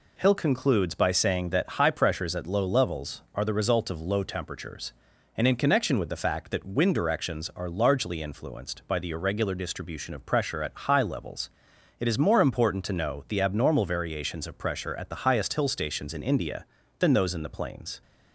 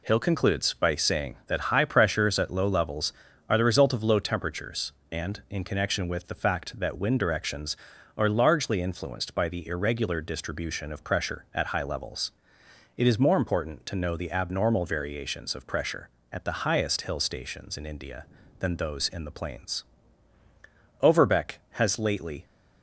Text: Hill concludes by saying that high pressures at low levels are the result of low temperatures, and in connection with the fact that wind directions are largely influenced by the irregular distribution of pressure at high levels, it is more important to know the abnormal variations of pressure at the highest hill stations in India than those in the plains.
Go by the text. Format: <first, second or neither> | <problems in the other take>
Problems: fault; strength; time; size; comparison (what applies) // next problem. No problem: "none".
first | goes on to say "Overbeck has lately"; from 21.0 s on; 1.4 s long